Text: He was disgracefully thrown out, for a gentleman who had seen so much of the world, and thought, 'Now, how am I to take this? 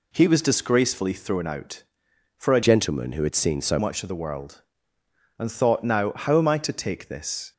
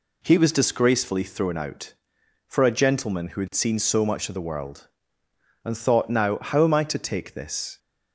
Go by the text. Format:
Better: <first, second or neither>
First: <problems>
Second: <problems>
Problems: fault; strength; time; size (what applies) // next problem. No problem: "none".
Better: second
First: changes voice from "gentleman" to "so"; from 2.6 to 3.7 s; 1.1 s long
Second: none